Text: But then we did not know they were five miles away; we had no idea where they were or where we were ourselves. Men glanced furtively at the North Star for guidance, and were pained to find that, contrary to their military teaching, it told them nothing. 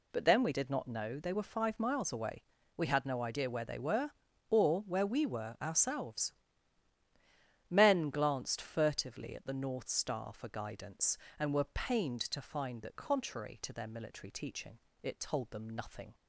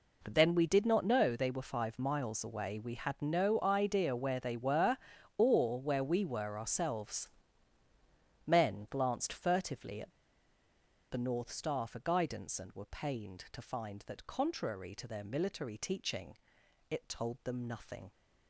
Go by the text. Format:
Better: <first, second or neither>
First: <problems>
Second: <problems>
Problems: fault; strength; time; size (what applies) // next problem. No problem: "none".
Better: first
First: none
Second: pauses between "at" and "the"; at 10.1 s; 0.99 s long